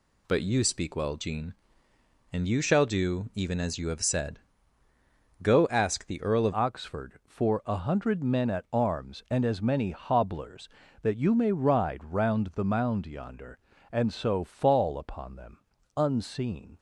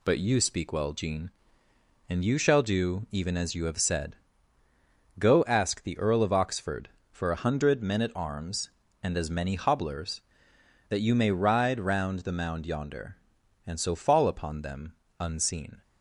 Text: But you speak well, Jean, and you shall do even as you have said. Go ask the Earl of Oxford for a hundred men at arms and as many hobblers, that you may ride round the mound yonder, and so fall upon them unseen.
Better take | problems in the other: second | changes voice at "Oxford"; from 6.5 s on; 10.2 s long // pauses between "them" and "unseen"; slight; at 15.5 s; 0.36 s long; slight in the second

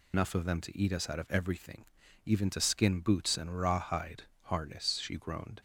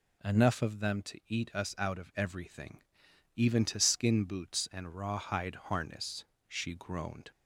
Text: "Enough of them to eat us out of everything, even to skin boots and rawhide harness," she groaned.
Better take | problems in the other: second | loses the start of "Enough"; at 0.1 s; 110 ms // pauses between "rawhide" and "harness"; slight; at 4.2 s; 0.20 s long

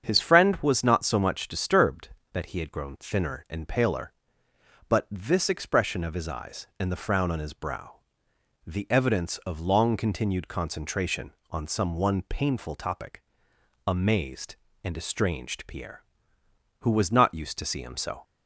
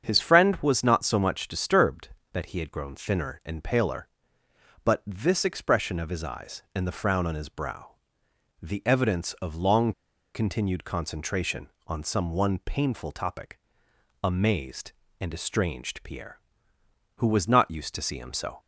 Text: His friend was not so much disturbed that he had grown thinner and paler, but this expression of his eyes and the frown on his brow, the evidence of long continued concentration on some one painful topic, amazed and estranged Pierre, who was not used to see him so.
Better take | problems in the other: first | starts louder than the rest; strong; until 1.0 s; 7.5 dB; strong in the first // pauses between "long" and "continued"; at 9.9 s; 0.42 s long

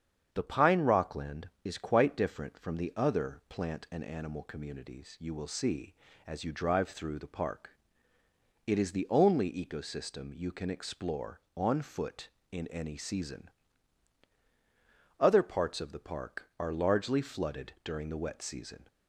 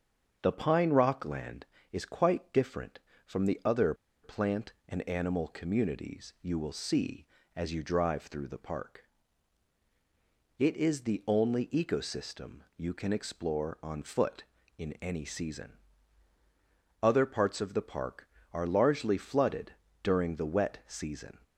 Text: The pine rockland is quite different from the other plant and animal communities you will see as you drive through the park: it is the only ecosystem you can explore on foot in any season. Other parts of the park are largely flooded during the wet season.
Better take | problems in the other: first | starts louder than the rest; until 1.4 s; 7 dB; strong in the first // pauses between "other" and "plant"; slight; at 3.9 s; 0.29 s long // pauses between "flooded" and "during"; slight; at 19.7 s; 0.28 s long

